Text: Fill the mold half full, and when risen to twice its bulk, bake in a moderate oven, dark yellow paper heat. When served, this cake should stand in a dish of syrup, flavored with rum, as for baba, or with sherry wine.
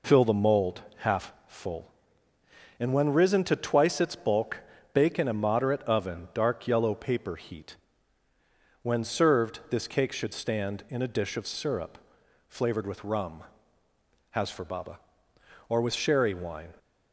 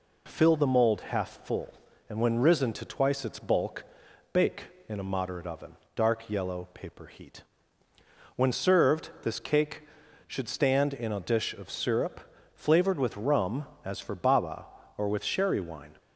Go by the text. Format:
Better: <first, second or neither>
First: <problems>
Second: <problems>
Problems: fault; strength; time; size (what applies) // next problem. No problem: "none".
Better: second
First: says "has" for "as"; at 14.3 s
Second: none